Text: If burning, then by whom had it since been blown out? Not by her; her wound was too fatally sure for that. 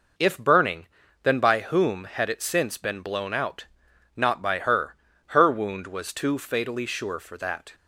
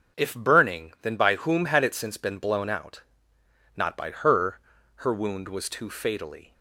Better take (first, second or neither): first